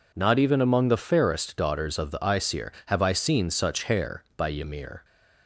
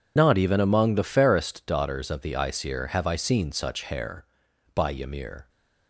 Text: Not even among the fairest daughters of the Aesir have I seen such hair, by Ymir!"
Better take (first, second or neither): first